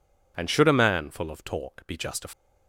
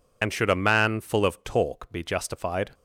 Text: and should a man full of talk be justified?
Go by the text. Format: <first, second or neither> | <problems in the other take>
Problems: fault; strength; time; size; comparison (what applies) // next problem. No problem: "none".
first | loses the start of "and"; at 0.2 s; 40 ms